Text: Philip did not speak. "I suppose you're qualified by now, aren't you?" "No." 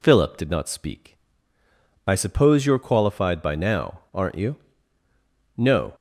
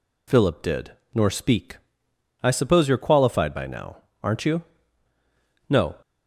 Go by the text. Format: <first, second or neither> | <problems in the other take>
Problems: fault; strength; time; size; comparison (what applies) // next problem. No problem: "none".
first | says "nor" for "not"; at 1.1 s